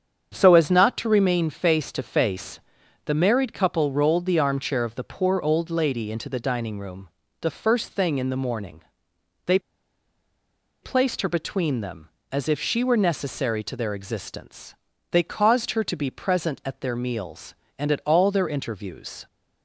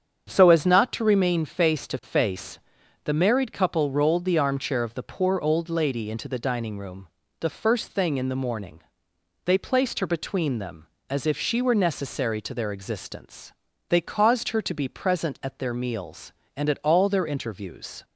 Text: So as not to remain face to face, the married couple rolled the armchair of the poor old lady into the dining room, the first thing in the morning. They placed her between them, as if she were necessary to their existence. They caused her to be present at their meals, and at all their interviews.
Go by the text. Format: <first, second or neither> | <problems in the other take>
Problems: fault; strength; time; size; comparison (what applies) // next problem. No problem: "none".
second | starts louder than the rest; strong; until 1.3 s; 7.5 dB; strong in the second // pauses between "They" and "placed"; at 9.5 s; 1.2 s long